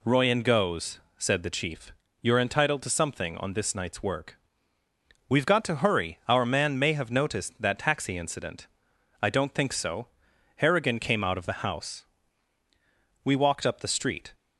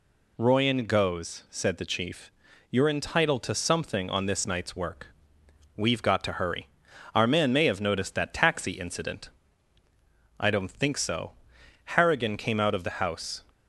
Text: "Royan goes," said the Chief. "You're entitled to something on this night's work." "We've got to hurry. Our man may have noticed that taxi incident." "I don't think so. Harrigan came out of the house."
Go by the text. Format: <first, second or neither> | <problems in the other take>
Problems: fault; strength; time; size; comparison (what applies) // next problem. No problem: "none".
second | goes on to say "We walked up the street"; noticeable; from 13.2 s on; 1.1 s long